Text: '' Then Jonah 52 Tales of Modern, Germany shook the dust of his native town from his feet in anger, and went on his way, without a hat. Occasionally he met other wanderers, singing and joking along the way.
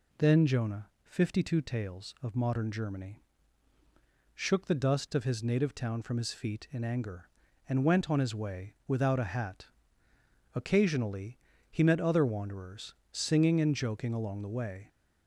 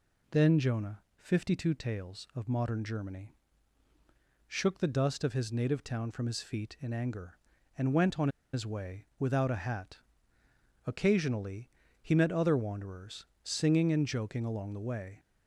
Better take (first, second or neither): first